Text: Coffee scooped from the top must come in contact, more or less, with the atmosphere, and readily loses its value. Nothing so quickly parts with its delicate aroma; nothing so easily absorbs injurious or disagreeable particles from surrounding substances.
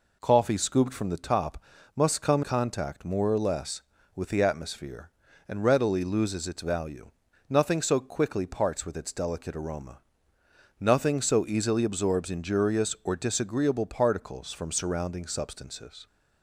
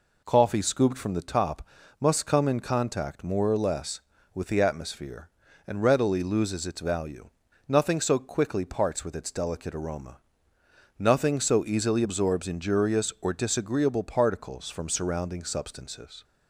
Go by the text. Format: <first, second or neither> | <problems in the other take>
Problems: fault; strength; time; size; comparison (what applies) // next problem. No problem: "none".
second | pauses between "top" and "must"; slight; at 1.6 s; 0.32 s long; slight in the second // skips "in"; at 2.4 s